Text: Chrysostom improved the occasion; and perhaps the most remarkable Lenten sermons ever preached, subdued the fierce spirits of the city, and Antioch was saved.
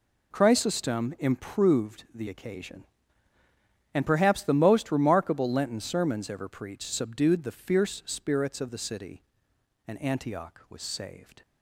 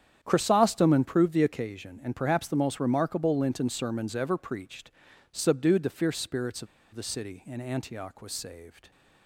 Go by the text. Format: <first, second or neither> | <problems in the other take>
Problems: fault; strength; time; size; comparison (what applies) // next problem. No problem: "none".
first | starts louder than the rest; strong; until 1.2 s; 9 dB // pauses between "of" and "the"; slight; at 6.6 s; 0.27 s long